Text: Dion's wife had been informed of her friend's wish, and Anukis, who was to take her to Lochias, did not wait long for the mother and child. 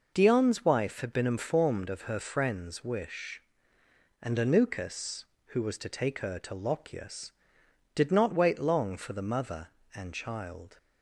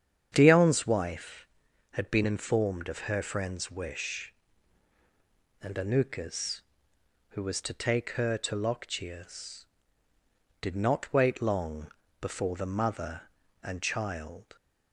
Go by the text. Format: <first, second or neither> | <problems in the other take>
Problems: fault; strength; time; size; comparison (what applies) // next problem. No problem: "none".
first | starts louder than the rest; strong; until 1.3 s; 8.5 dB // says "before" for "for"; at 12.2 s